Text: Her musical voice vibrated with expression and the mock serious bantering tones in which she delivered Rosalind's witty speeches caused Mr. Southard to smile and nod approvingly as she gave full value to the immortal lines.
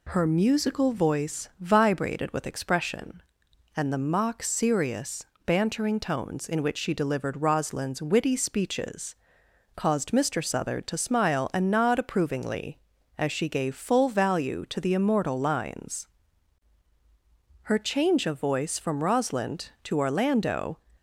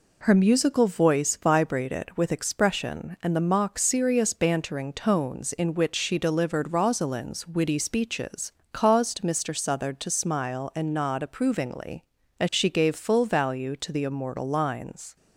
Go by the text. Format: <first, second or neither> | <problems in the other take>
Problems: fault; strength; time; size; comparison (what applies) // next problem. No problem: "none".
second | pauses between "serious" and "bantering"; slight; at 5.2 s; 0.20 s long // pauses between "speeches" and "caused"; noticeable; at 9.1 s; 0.60 s long; slight in the second // goes on to say "Her change of voice from Rosalind to Orlando"; strong; from 17.6 s on; 3.1 s long